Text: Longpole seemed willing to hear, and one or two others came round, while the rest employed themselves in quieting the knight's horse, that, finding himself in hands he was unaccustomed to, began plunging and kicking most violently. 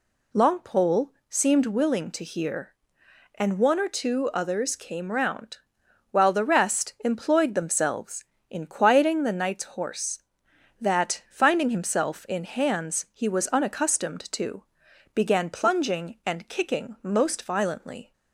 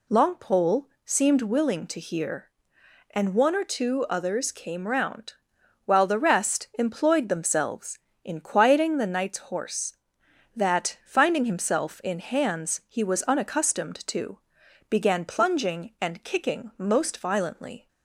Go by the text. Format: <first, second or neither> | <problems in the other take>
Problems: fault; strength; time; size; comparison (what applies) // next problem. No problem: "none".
neither | pauses between "Longpole" and "seemed"; slight; the same in both